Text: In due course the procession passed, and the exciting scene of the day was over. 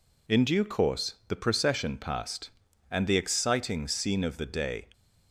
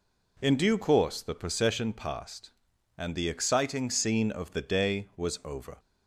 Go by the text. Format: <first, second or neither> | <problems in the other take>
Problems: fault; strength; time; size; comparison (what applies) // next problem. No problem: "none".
second | stops before "was over"; at 4.9 s